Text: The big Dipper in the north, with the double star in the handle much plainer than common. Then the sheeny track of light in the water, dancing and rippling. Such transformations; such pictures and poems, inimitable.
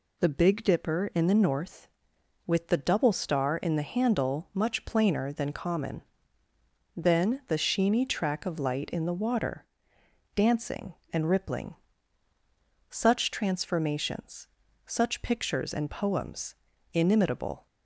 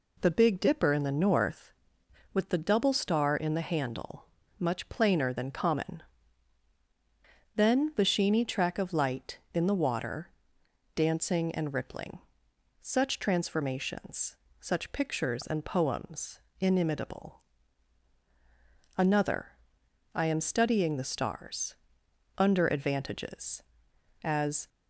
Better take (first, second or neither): first